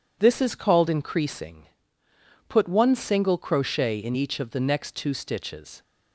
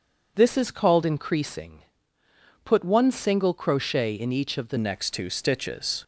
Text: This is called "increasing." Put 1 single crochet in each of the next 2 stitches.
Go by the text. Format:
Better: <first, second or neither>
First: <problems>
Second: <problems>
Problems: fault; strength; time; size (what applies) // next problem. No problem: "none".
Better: first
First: none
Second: changes voice at "next"; from 4.7 s on; 1.3 s long